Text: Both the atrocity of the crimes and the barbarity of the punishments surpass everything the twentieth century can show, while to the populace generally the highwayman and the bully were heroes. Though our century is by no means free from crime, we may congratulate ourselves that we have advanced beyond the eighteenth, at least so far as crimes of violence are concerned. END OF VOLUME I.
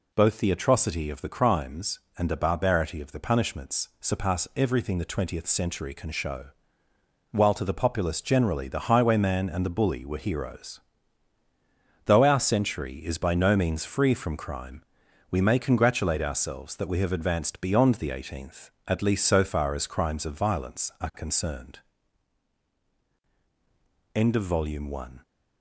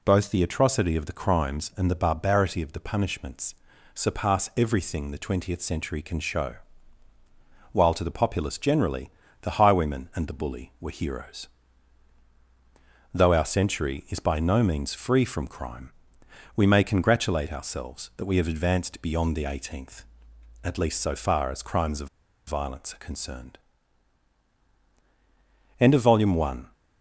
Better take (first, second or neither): first